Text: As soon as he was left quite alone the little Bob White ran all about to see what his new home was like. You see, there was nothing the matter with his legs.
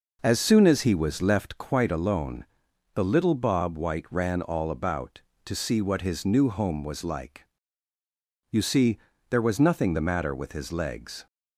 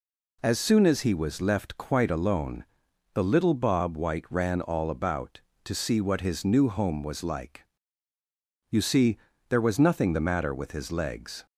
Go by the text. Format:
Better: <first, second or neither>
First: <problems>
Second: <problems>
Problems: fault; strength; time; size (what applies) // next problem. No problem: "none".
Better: second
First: starts louder than the rest; noticeable; until 1.5 s; 5 dB // pauses between "alone" and "the"; noticeable; at 2.4 s; 0.50 s long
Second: pauses between "alone" and "the"; noticeable; at 2.6 s; 0.50 s long